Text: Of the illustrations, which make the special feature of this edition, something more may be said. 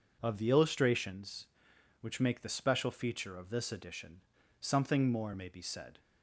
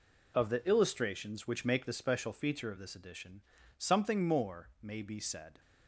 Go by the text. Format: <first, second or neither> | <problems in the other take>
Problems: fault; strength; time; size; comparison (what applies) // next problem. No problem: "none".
neither | none